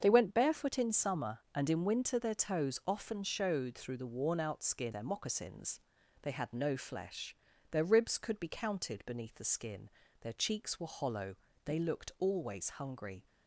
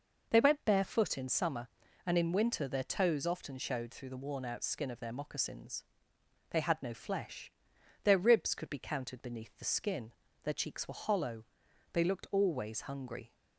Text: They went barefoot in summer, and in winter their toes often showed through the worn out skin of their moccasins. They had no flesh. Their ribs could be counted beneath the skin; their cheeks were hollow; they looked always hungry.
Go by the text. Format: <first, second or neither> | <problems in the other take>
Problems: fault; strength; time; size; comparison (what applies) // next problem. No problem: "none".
second | starts louder than the rest; until 1.0 s; 7 dB // skips "of"; at 4.9 s